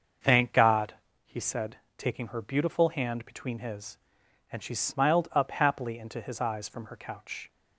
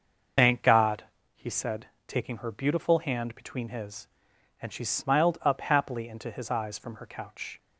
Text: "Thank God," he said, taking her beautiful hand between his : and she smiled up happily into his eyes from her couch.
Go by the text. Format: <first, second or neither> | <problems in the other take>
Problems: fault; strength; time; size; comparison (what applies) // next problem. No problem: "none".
first | loses the start of "Thank"; at 0.3 s; 50 ms // starts louder than the rest; until 1.7 s; 6.5 dB; also in the first